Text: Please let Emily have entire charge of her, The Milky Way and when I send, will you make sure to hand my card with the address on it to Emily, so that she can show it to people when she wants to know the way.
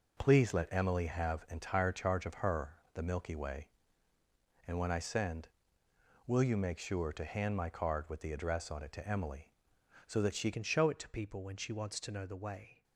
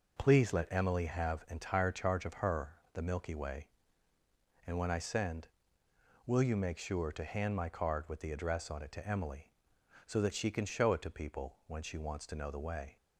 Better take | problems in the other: second | changes voice at "can"; from 10.5 s on; 2.3 s long

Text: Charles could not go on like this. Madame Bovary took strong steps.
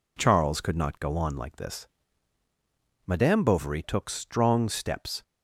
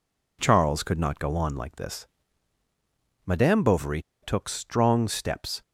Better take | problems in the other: first | pauses between "Bovary" and "took"; slight; at 4.0 s; 0.20 s long

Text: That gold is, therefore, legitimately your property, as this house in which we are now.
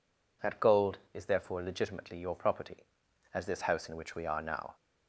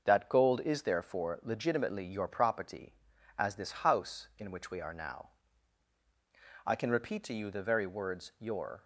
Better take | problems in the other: first | starts louder than the rest; noticeable; until 1.0 s; 6 dB // goes on to say "I can repeat to you the very words your"; strong; from 6.6 s on; 2.1 s long

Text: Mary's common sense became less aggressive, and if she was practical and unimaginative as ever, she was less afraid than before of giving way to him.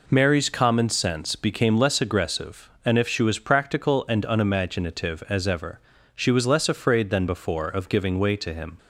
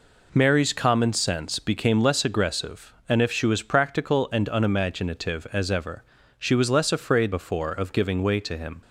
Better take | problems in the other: first | skips "than"; at 7.3 s

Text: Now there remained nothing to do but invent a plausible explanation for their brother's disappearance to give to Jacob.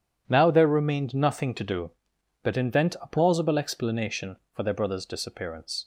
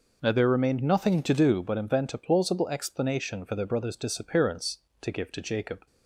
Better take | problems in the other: second | stops before "to give to Jacob"; at 5.8 s

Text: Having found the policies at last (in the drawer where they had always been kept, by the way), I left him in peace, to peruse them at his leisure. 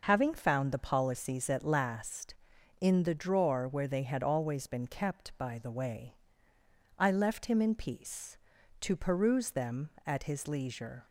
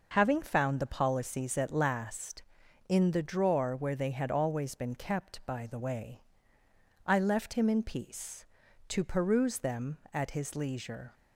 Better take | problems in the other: neither | none

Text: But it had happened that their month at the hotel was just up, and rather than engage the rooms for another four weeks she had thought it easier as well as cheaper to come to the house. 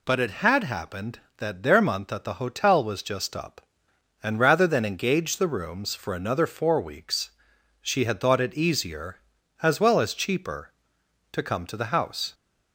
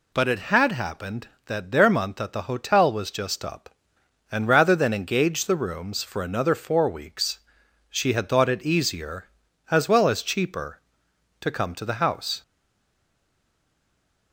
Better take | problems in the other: first | pauses between "weeks" and "she"; noticeable; at 7.3 s; 0.56 s long; noticeable in the first // stays silent after the last word; noticeable; from 12.4 s on; 1.9 s long

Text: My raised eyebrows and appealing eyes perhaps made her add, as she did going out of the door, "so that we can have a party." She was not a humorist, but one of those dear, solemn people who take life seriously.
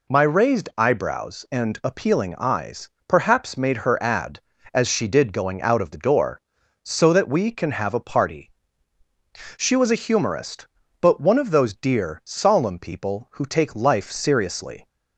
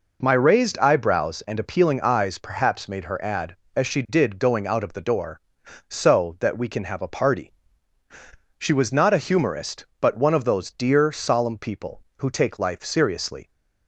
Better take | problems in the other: second | pauses between "eyes" and "perhaps"; slight; at 2.8 s; 0.18 s long // skips "not"; at 9.9 s

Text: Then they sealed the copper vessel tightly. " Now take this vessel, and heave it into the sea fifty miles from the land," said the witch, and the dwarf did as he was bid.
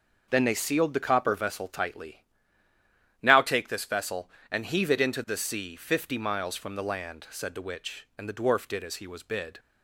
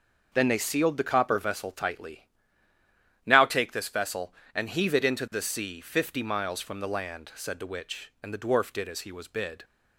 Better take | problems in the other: neither | none

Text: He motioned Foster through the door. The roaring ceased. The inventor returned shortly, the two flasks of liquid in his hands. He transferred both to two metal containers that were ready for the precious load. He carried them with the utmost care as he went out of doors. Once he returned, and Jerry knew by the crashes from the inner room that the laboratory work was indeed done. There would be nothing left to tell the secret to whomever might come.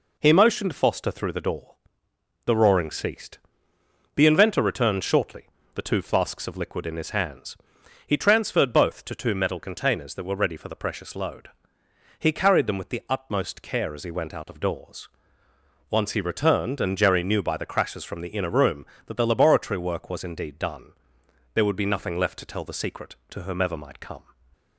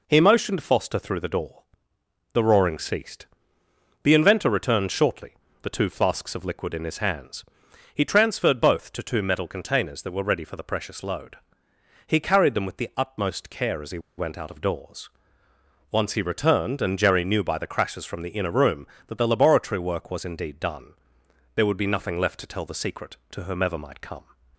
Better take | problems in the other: first | pauses between "he" and "went"; slight; at 13.9 s; 0.18 s long

